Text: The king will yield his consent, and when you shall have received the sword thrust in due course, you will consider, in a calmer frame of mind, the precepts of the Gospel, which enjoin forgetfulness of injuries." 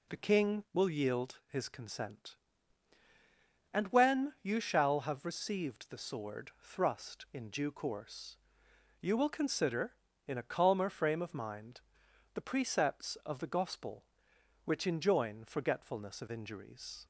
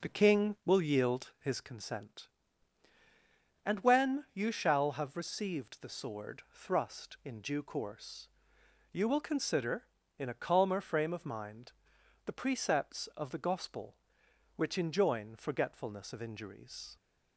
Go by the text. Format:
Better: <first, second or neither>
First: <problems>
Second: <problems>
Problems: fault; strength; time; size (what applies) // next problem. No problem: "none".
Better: first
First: none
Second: starts louder than the rest; noticeable; until 1.6 s; 4.5 dB